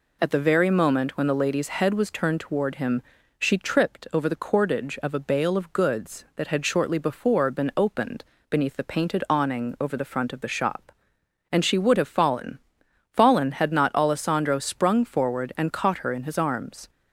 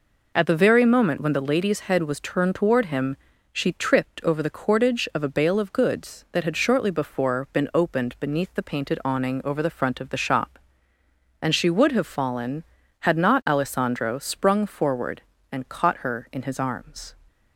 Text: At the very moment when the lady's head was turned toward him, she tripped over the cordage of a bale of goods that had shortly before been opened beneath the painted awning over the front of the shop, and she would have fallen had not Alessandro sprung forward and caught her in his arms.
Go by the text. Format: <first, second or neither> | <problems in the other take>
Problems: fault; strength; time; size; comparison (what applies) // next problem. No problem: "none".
second | pauses between "opened" and "beneath"; slight; at 8.2 s; 0.24 s long // says "fallen" twice; at 13.1 s